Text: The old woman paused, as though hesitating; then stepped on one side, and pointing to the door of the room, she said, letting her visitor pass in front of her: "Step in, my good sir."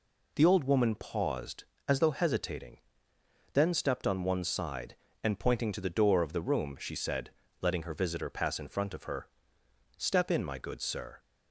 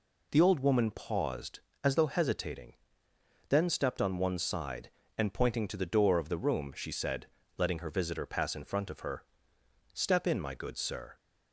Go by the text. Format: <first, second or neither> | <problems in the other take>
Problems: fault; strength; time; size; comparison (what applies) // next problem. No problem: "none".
neither | none